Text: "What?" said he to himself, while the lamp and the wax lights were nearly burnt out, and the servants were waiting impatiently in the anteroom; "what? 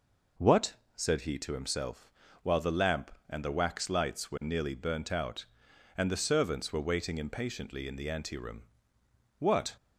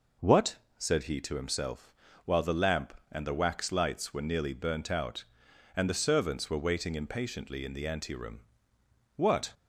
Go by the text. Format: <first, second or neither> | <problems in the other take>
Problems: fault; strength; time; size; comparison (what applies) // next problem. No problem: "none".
neither | none